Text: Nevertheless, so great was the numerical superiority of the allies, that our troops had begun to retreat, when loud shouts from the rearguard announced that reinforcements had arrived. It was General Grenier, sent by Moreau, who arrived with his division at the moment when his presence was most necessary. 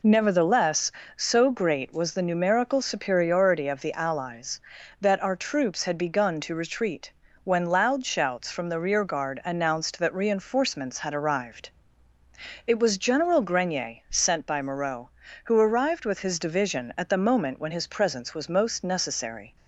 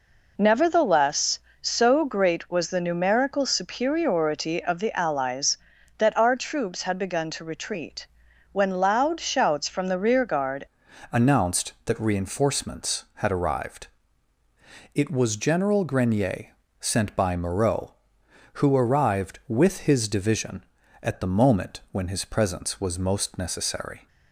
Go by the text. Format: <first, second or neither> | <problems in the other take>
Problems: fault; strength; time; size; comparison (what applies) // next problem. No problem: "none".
first | changes voice at "announced"; from 11.1 s on; 12.9 s long